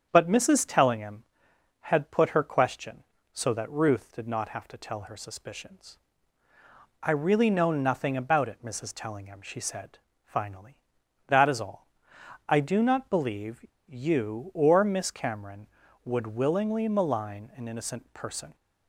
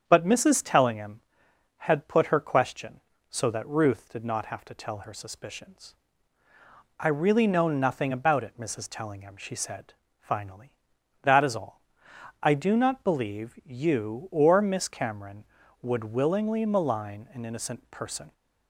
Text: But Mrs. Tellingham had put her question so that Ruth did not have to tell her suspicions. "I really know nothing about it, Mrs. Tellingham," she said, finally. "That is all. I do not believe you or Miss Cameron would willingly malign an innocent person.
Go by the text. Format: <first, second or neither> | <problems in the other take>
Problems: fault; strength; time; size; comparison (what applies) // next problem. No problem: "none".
second | starts louder than the rest; strong; until 1.1 s; 8 dB; strong in the second // pauses between "believe" and "you"; slight; at 13.6 s; 0.22 s long